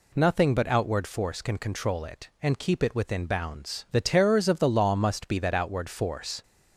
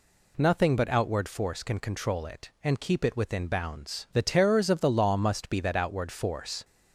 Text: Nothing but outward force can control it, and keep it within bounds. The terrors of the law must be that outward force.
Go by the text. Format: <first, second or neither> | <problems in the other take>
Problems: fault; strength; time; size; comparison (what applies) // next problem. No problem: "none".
neither | none